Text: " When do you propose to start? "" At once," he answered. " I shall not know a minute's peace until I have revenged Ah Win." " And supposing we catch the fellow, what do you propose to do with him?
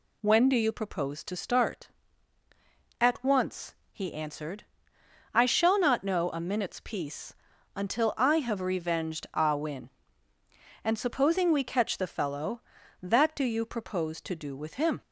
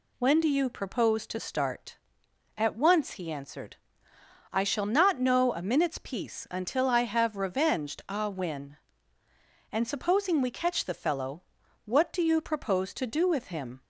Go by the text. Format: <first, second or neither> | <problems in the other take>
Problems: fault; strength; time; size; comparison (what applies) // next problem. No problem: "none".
second | pauses between "peace" and "until"; at 7.3 s; 0.42 s long // says "that" for "what"; at 13.0 s